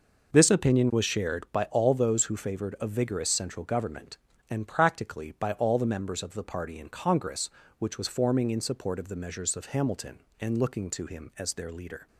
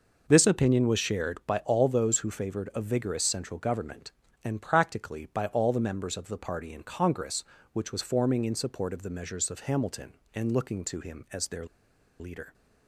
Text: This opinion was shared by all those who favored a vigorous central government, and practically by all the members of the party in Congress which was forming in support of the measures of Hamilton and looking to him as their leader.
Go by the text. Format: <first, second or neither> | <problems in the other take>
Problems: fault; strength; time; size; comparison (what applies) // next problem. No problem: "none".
first | pauses between "their" and "leader"; noticeable; at 11.6 s; 0.54 s long